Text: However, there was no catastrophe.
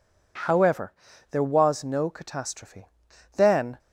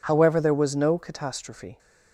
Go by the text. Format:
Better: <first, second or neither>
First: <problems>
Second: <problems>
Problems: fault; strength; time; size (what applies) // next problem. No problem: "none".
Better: second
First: goes on to say "Then"; slight; from 3.3 s on; 0.42 s long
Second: none